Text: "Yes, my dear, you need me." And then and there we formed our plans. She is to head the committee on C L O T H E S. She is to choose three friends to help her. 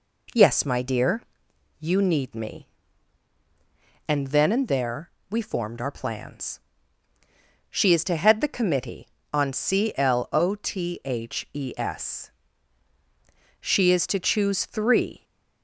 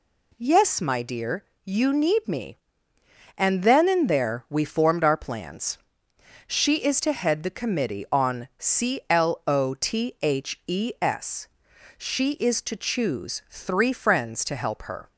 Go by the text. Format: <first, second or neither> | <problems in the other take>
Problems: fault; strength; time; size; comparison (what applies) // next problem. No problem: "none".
second | pauses between "there" and "we"; slight; at 5.0 s; 0.22 s long // stops before "friends to help her"; at 15.2 s